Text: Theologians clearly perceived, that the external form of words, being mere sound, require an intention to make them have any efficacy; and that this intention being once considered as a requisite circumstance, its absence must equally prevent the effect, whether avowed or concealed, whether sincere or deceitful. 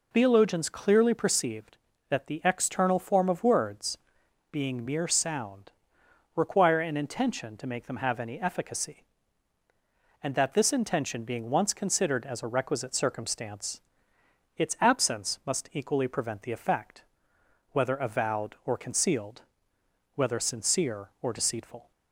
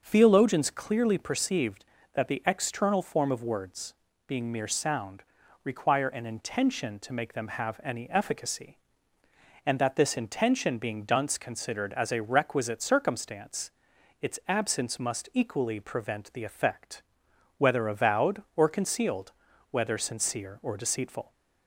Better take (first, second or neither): first